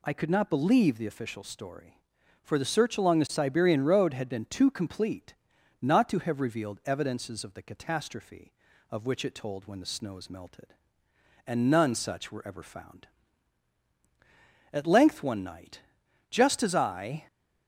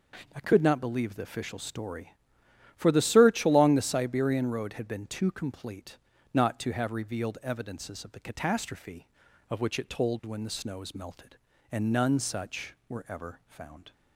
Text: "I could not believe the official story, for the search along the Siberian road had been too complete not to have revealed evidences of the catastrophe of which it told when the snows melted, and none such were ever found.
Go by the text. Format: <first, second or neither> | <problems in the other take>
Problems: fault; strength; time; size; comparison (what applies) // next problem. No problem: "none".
second | pauses between "complete" and "not"; noticeable; at 5.3 s; 0.46 s long; slight in the second // goes on to say "At length one night just as I"; strong; from 14.7 s on; 2.5 s long